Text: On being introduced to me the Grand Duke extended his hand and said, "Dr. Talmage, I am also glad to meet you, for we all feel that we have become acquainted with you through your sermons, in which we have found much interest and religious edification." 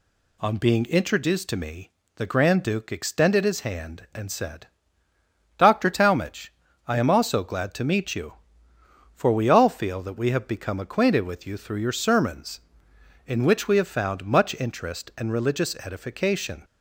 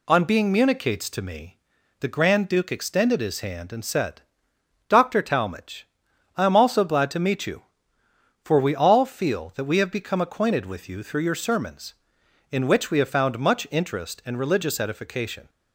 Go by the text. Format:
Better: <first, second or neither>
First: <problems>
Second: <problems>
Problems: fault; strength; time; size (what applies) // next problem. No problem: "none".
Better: first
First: pauses between "me" and "the"; slight; at 1.8 s; 0.26 s long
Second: says "municates" for "introduced"; at 0.5 s // pauses between "me" and "the"; at 1.5 s; 0.44 s long